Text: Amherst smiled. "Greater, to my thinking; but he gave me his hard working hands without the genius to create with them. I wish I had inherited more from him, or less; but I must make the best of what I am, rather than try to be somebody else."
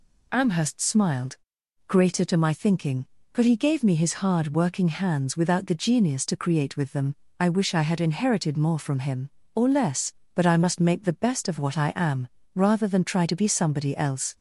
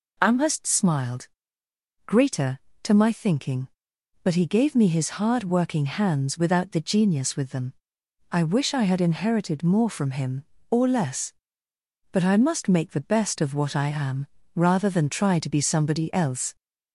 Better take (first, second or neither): first